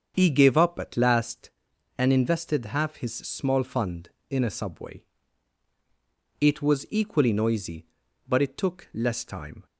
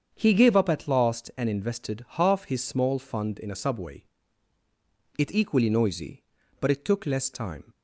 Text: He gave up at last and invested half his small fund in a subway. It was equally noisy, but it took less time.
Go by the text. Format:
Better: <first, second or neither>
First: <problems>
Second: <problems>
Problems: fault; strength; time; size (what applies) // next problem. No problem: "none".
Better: first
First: starts louder than the rest; strong; until 1.1 s; 7 dB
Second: starts louder than the rest; strong; until 1.1 s; 7.5 dB // skips "was"; at 5.3 s